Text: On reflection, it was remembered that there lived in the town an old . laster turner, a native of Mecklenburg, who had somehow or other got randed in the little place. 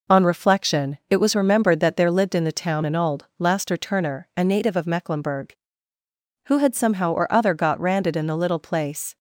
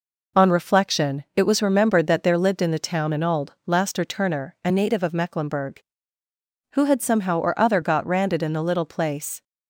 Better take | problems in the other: neither | none

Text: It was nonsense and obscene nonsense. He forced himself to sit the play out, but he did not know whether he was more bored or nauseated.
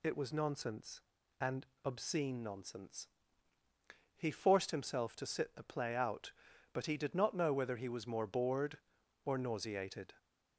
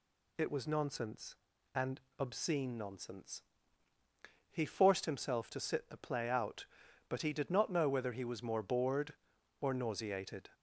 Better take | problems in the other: neither | pauses between "and" and "obscene"; slight; the same in both

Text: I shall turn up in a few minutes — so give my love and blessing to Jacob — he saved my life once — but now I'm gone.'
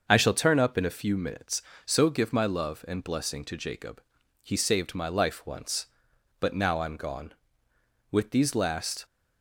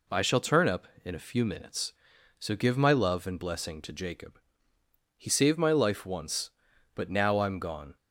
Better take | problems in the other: second | starts louder than the rest; until 1.0 s; 6.5 dB // goes on to say "With these last"; noticeable; from 8.1 s on; 0.94 s long

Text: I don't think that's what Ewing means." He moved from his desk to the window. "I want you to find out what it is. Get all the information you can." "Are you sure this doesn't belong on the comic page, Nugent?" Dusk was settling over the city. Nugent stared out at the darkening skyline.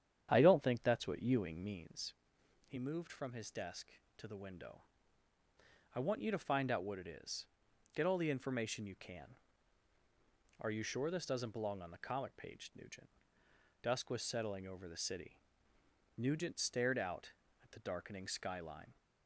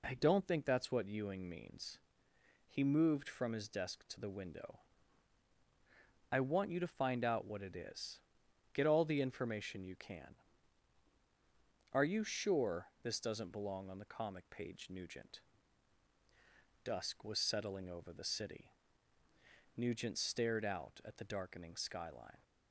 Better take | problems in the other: second | starts louder than the rest; strong; until 2.0 s; 9.5 dB

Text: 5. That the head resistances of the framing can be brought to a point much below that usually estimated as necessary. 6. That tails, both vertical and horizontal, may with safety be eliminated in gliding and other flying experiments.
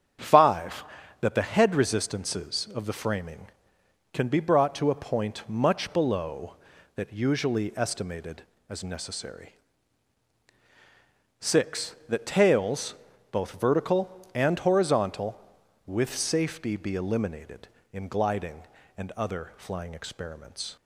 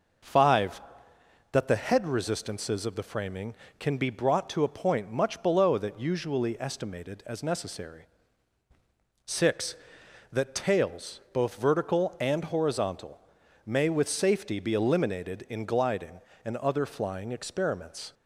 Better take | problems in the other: second | starts louder than the rest; strong; until 1.5 s; 8 dB // skips "may"; at 15.6 s

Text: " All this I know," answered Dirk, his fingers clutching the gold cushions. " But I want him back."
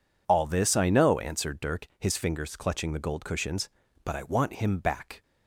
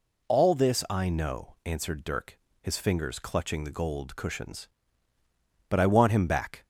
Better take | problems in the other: neither | none

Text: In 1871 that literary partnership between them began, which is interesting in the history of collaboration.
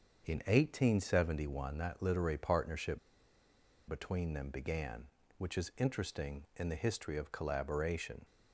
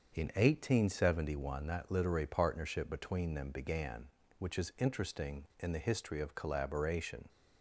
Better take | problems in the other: second | starts louder than the rest; until 1.3 s; 6.5 dB; also in the second // pauses between "partnership" and "between"; noticeable; at 2.9 s; 0.89 s long

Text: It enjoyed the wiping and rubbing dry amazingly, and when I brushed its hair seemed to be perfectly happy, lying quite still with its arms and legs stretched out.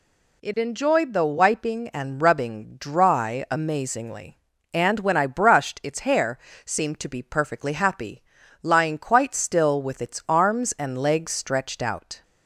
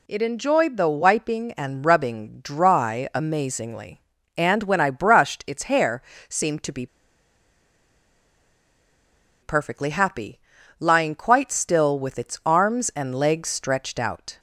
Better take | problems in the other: first | pauses between "hair" and "seemed"; slight; at 6.0 s; 0.26 s long; slight in the first // pauses between "be" and "perfectly"; strong; at 6.8 s; 2.5 s long

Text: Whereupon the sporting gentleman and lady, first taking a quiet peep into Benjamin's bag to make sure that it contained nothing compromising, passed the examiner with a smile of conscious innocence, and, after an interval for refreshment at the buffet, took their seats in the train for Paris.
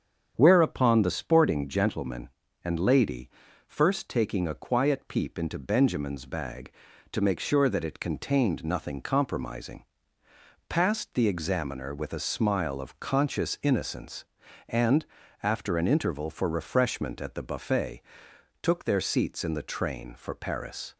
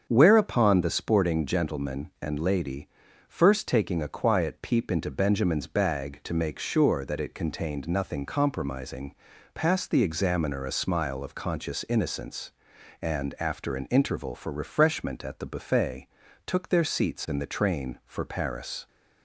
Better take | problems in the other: first | starts louder than the rest; until 1.1 s; 7 dB; strong in the first // skips "with"; at 10.6 s

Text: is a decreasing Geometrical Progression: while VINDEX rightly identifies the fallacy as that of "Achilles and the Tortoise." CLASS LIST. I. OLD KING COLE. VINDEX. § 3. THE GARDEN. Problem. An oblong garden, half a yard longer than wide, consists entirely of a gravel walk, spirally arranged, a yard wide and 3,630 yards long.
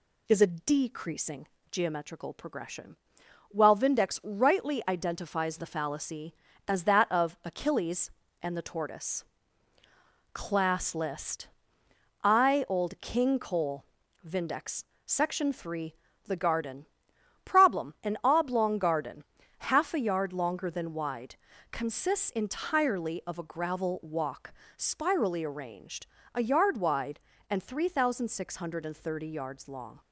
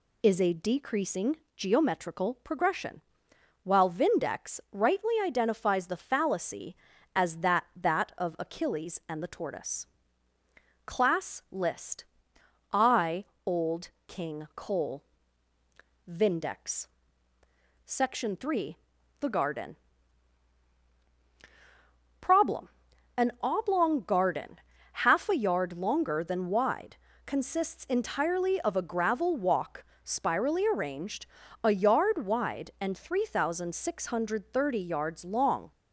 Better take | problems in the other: first | pauses between "decreasing" and "Geometrical"; slight; at 1.3 s; 0.20 s long; slight in the first // says "that" twice; at 7.7 s // pauses between "OLD" and "KING"; slight; at 13.8 s; 0.20 s long

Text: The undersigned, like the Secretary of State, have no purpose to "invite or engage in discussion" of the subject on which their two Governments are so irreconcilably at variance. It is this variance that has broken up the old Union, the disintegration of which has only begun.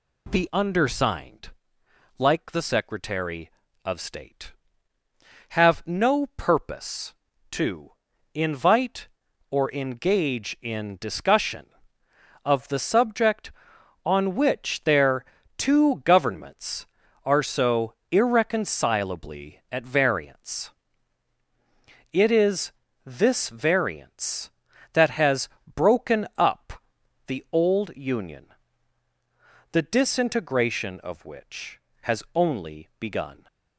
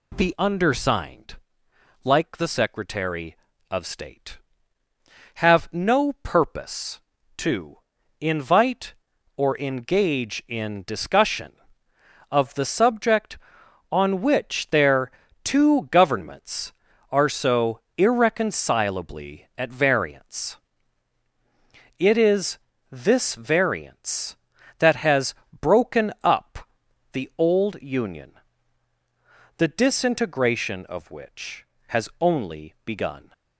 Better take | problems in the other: neither | pauses between "to" and "invite"; the same in both // pauses between "their" and "two"; slight; the same in both // pauses between "so" and "irreconcilably"; slight; the same in both // pauses between "is" and "this"; slight; the same in both // pauses between "has" and "broken"; slight; the same in both // pauses between "up" and "the"; the same in both

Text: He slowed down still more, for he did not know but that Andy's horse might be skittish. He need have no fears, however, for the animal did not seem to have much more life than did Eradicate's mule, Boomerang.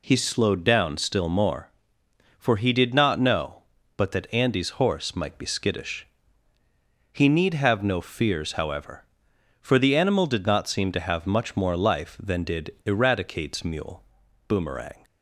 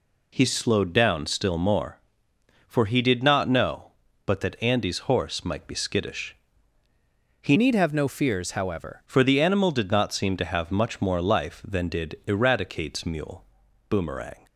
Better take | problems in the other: first | changes voice from "need" to "however"; from 7.5 to 9.0 s; 1.5 s long

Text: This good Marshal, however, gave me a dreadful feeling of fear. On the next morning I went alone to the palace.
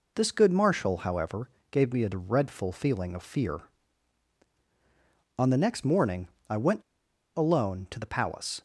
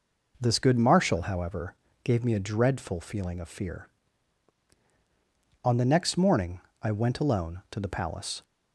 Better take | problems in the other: second | pauses between "morning" and "I"; slight; at 6.2 s; 0.20 s long; slight in the second // pauses between "went" and "alone"; noticeable; at 6.8 s; 0.54 s long

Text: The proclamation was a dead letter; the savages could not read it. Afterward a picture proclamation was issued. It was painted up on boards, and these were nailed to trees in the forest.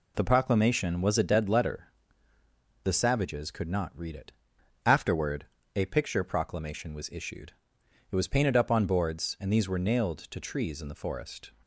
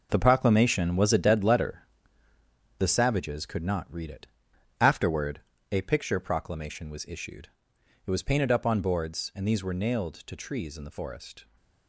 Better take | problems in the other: first | gets quieter; strong; throughout; 10 dB // pauses between "Afterward" and "a"; slight; at 5.4 s; 0.30 s long; slight in the first

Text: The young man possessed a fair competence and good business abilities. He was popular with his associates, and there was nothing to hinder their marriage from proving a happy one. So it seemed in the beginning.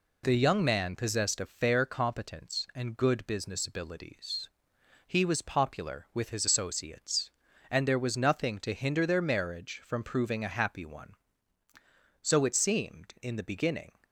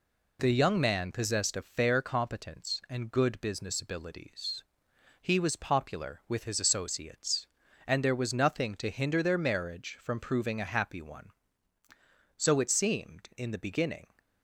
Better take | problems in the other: neither | none

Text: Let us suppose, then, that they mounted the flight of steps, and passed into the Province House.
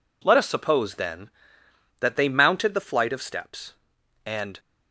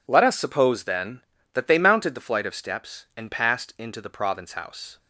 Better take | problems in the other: second | stops before "passed into the Province House"; at 4.5 s

